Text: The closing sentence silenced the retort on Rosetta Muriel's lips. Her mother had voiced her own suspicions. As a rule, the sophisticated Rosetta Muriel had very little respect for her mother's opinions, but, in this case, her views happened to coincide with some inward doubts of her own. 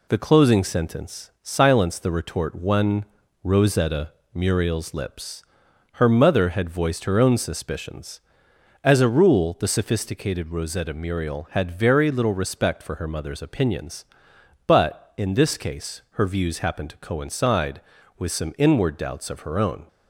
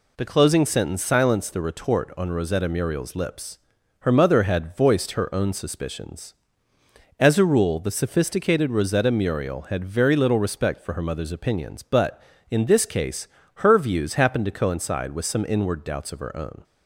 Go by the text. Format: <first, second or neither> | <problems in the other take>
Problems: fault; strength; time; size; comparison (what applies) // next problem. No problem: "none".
second | says "one" for "on"; at 2.5 s // pauses between "Rosetta" and "Muriel's"; slight; at 4.1 s; 0.22 s long